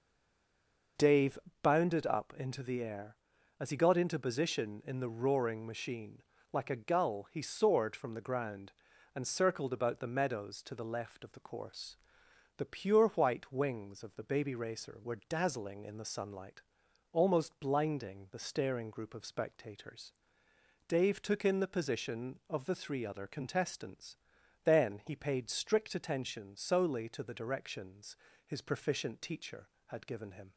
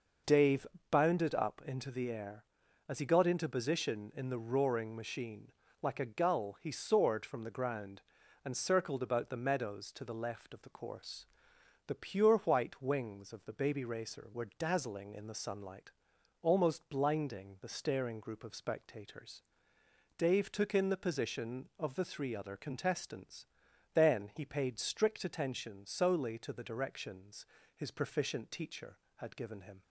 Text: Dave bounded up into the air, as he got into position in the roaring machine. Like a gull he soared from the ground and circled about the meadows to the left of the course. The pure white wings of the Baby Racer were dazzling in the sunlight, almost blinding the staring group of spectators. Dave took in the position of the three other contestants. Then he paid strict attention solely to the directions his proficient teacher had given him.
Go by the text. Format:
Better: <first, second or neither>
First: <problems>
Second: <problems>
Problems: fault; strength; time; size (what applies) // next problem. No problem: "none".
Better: second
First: stays silent before the first word; until 0.9 s; 0.9 s long // pauses between "Dave" and "bounded"; slight; at 1.3 s; 0.24 s long // pauses between "directions" and "his"; slight; at 28.1 s; 0.32 s long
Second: pauses between "Dave" and "bounded"; slight; at 0.6 s; 0.24 s long // pauses between "directions" and "his"; slight; at 27.4 s; 0.32 s long